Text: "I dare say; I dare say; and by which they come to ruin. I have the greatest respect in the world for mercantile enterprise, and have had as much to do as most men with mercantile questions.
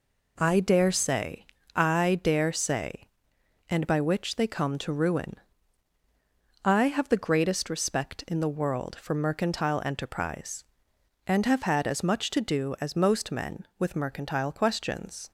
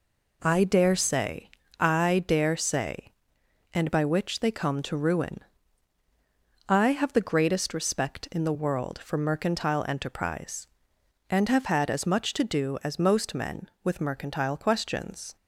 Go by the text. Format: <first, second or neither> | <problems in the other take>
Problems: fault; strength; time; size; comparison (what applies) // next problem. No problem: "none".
neither | none